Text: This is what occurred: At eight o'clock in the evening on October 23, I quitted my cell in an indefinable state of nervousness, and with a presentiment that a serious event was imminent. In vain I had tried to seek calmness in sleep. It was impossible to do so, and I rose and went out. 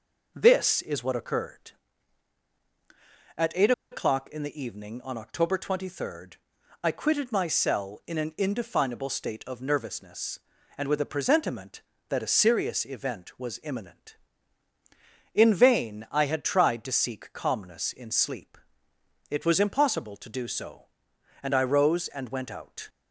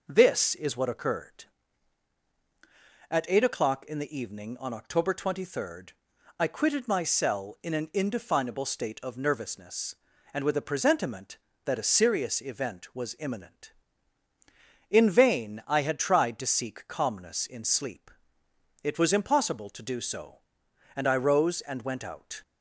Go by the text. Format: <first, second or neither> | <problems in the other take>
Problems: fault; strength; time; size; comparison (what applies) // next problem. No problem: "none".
second | pauses between "eight" and "o'clock"; slight; at 3.7 s; 0.20 s long